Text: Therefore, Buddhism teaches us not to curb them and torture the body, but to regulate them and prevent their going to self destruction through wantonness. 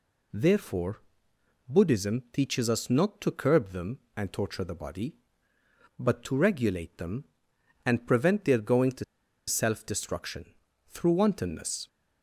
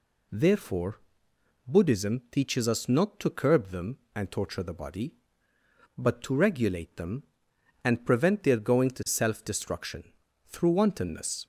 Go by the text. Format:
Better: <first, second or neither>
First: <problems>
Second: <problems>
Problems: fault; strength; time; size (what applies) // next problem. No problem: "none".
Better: second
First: pauses between "to" and "self"; at 9.0 s; 0.43 s long // pauses between "destruction" and "through"; at 10.4 s; 0.44 s long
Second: pauses between "destruction" and "through"; at 10.0 s; 0.44 s long